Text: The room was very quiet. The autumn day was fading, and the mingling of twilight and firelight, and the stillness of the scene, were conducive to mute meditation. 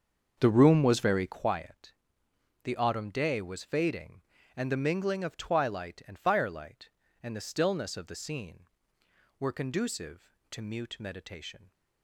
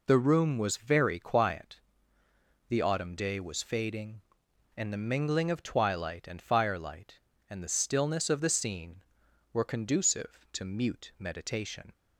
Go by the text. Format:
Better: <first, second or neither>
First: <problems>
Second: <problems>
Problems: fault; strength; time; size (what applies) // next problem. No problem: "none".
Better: second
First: starts louder than the rest; until 1.5 s; 6.5 dB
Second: none